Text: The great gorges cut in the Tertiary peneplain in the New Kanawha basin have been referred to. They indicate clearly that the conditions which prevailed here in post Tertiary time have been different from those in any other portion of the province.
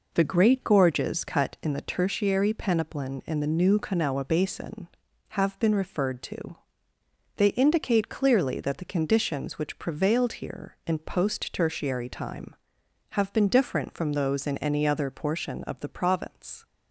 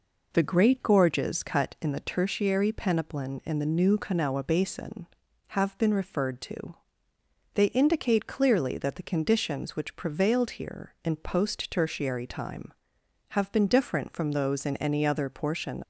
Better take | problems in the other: first | stops before "of the province"; at 15.8 s

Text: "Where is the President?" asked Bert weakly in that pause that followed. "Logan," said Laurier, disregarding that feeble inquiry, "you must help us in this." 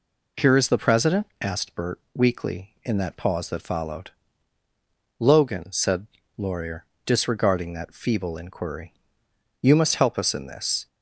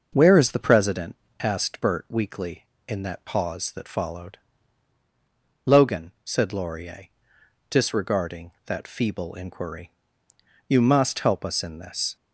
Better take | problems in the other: second | says "Here" for "Where"; at 0.3 s // pauses between "said" and "Laurier"; slight; at 6.0 s; 0.30 s long

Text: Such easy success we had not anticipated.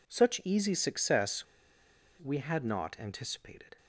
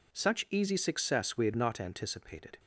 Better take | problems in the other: second | pauses between "success" and "we"; noticeable; at 1.4 s; 0.75 s long

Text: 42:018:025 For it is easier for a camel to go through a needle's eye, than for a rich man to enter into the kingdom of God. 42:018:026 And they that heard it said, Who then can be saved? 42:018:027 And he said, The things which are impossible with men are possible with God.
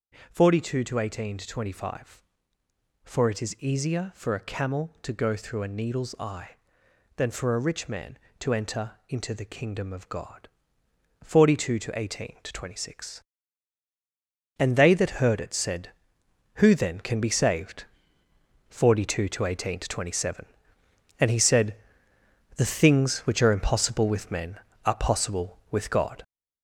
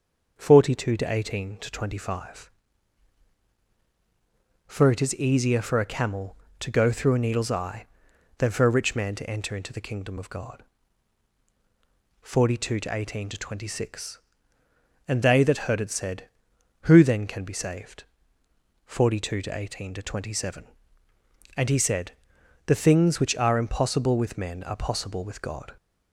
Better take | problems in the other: second | gets louder; noticeable; throughout; 5.5 dB // starts louder than the rest; noticeable; until 1.3 s; 6 dB; noticeable in the second // pauses between "enter" and "into"; slight; at 8.9 s; 0.15 s long

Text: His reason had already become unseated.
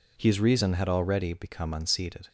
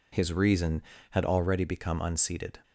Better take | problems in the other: neither | none

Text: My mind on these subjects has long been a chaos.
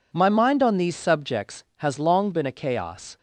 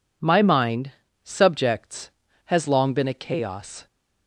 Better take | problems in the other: first | skips "on these"; at 1.0 s

